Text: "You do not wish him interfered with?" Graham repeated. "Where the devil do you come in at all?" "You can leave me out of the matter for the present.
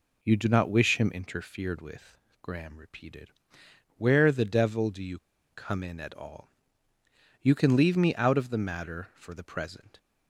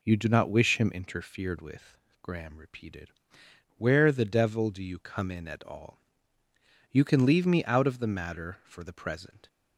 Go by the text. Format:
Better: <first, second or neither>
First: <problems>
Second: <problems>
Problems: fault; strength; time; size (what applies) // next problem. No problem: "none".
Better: second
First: pauses between "you" and "come"; slight; at 5.1 s; 0.34 s long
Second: none